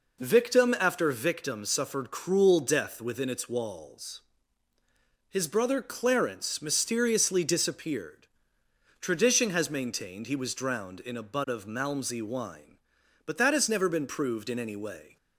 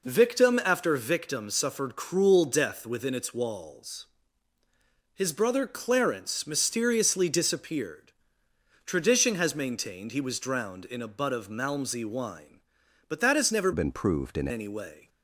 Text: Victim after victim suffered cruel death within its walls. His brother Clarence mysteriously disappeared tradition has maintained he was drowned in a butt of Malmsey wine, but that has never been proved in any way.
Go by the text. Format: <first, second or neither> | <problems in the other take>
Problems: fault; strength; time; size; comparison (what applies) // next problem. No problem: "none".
first | pauses between "disappeared" and "tradition"; noticeable; at 7.9 s; 0.86 s long; noticeable in the first // changes voice from "been" to "in"; from 13.7 to 14.4 s; 0.7 s long